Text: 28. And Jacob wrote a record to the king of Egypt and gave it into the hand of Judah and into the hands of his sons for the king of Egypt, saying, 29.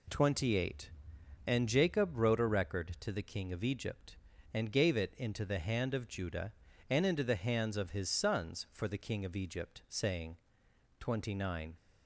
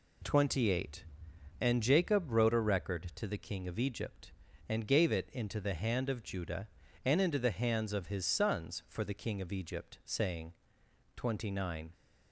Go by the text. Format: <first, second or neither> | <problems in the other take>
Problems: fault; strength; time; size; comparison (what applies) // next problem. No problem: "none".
neither | none